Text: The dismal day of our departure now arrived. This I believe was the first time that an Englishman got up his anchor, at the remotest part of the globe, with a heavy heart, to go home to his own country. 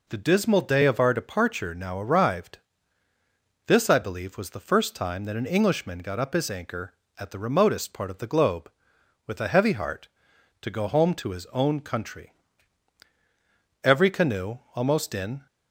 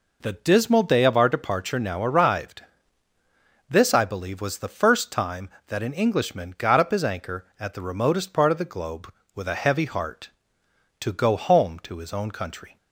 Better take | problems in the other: second | goes on to say "Every canoe almost in"; from 13.8 s on; 1.6 s long

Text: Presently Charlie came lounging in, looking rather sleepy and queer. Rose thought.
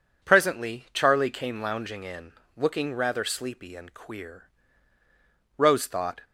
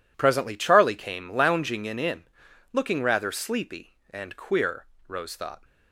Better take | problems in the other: first | says "in" twice; at 1.9 s

